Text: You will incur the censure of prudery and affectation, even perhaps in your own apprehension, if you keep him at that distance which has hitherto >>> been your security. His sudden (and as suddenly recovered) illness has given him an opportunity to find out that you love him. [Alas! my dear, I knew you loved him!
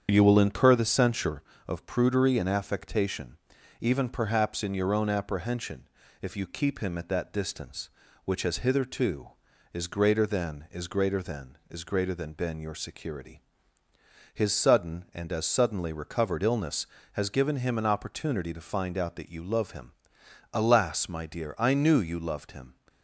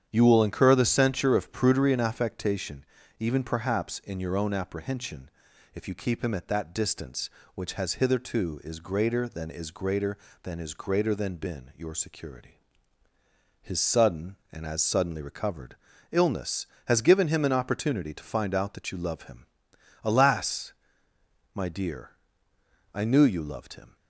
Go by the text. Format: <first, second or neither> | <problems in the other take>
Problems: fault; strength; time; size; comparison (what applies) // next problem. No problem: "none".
neither | starts louder than the rest; strong; the same in both